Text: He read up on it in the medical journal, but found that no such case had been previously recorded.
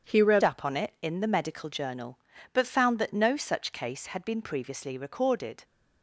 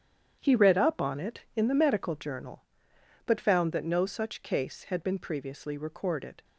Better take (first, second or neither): second